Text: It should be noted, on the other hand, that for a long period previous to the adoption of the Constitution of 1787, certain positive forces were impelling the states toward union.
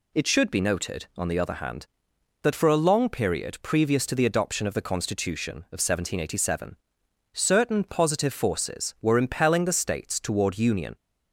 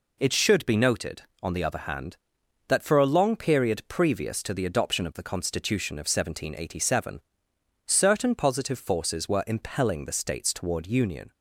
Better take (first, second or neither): neither